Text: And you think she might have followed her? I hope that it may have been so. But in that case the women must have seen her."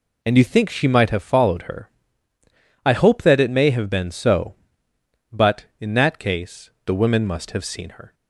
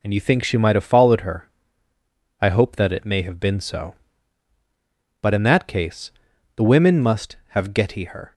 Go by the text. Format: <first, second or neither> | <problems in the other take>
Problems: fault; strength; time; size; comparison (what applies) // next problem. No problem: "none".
first | pauses between "case" and "the"; at 6.1 s; 0.44 s long; slight in the first // says "getty" for "seen"; at 7.7 s